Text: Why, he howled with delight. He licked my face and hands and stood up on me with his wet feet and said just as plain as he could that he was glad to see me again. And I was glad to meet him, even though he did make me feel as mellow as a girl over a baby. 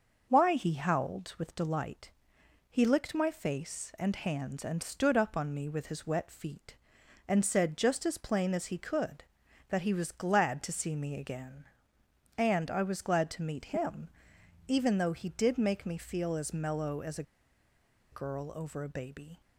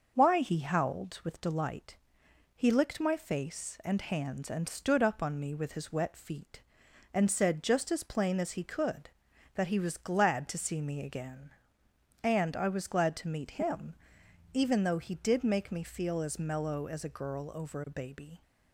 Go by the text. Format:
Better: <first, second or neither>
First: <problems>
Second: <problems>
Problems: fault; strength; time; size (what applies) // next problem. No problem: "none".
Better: second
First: starts louder than the rest; noticeable; until 1.3 s; 6 dB // pauses between "a" and "girl"; noticeable; at 17.2 s; 0.88 s long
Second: starts louder than the rest; noticeable; until 1.1 s; 6 dB